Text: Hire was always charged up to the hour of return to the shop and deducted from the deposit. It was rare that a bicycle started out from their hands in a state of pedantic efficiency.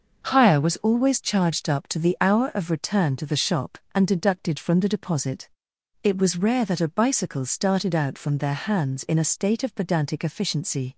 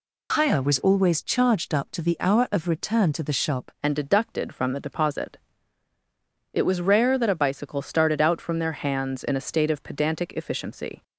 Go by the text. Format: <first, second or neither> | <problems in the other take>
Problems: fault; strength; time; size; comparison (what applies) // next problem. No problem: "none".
first | changes voice at "and"; from 3.8 s on; 7.2 s long